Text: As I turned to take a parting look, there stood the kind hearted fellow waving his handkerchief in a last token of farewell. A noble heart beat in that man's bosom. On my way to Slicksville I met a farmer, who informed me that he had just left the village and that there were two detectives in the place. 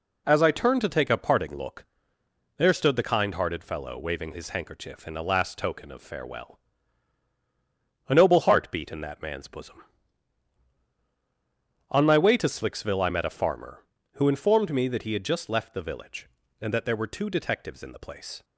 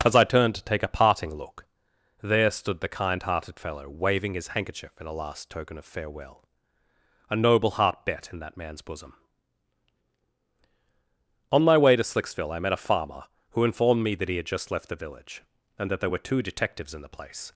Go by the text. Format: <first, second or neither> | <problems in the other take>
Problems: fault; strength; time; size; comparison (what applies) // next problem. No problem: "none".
first | says "bet" for "beat"; at 8.0 s